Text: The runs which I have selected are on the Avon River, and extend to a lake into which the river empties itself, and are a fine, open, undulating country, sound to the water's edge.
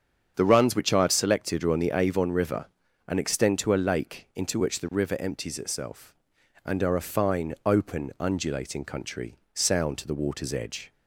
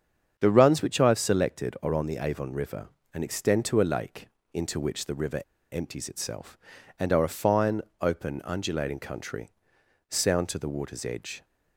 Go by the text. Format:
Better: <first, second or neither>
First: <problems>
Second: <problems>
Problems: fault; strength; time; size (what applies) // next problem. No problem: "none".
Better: first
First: starts louder than the rest; strong; until 1.3 s; 7.5 dB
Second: starts louder than the rest; strong; until 1.3 s; 7.5 dB // pauses between "lake" and "into"; slight; at 4.2 s; 0.26 s long // pauses between "river" and "empties"; slight; at 5.4 s; 0.30 s long